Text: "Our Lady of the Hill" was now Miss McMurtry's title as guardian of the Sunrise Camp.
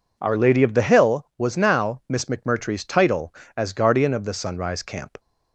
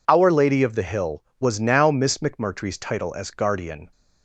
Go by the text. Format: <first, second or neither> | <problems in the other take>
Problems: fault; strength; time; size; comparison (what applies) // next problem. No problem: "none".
first | stops before "of the Sunrise Camp"; at 3.9 s